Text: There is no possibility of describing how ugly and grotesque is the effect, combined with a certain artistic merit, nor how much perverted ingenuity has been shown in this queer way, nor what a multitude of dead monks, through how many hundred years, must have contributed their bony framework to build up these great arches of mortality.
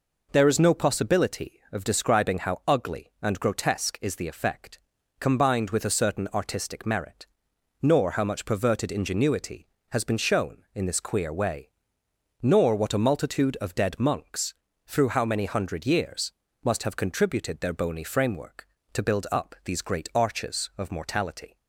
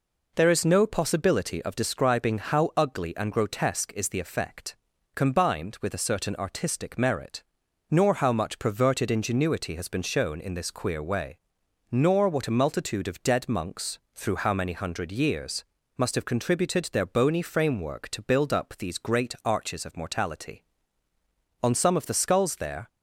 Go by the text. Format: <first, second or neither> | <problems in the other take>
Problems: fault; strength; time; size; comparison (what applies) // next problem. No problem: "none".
first | goes on to say "On some of the skulls there"; noticeable; from 21.6 s on; 1.2 s long